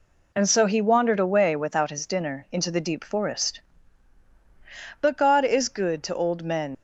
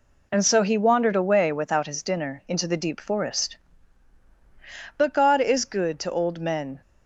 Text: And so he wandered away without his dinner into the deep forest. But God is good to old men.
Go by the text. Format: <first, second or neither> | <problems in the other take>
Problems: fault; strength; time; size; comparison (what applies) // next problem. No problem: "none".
second | leaves "men" unfinished; at 6.7 s; 95 ms